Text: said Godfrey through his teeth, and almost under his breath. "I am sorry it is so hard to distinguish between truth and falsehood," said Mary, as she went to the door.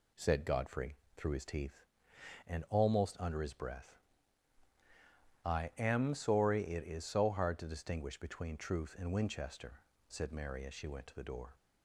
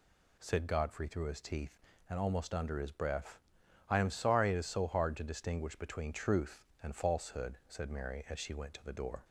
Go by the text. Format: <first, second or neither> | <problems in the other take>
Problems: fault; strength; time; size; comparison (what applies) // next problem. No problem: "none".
second | pauses between "Godfrey" and "through"; slight; at 0.9 s; 0.20 s long // says "winchester" for "falsehood"; at 9.1 s